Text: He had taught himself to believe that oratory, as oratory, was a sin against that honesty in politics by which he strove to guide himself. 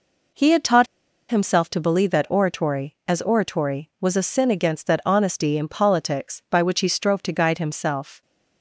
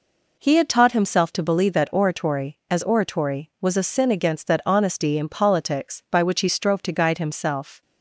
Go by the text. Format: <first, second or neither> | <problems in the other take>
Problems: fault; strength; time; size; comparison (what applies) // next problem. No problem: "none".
second | pauses between "taught" and "himself"; at 0.8 s; 0.42 s long